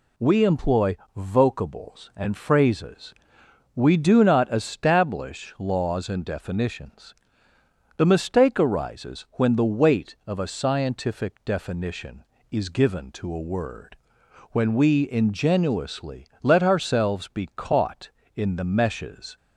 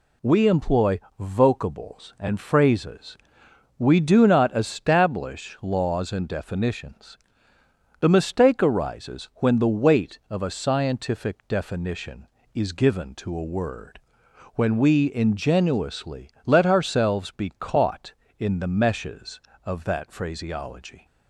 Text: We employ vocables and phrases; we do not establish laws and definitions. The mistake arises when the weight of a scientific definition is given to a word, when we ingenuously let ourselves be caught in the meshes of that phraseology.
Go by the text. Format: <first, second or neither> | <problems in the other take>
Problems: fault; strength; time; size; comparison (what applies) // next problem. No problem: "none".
second | pauses between "employ" and "vocables"; slight; at 0.9 s; 0.18 s long; slight in the second // pauses between "ingenuously" and "let"; slight; at 16.2 s; 0.16 s long; slight in the second // stops before "of that phraseology"; at 19.3 s